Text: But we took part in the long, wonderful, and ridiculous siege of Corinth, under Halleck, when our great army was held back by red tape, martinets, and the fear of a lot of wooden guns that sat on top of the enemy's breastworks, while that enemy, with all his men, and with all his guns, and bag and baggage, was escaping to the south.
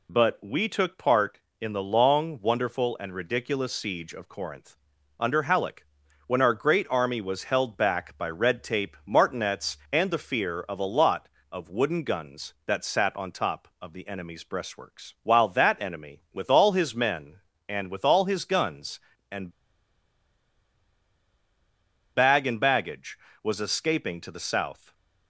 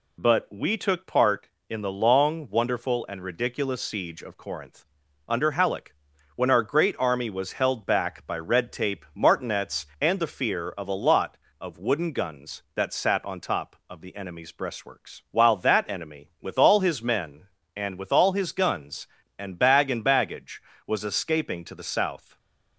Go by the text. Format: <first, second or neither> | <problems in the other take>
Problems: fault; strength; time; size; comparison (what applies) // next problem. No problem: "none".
second | pauses between "and" and "bag"; strong; at 19.5 s; 2.6 s long